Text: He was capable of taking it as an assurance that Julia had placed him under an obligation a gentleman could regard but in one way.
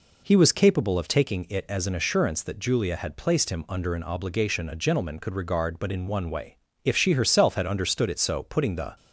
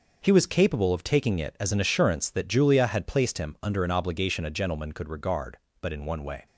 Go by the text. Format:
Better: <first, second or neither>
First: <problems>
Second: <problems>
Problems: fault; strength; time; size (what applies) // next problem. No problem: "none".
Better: second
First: goes on to say "If she herself had understood it so putting the"; strong; from 6.8 s on; 2.1 s long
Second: none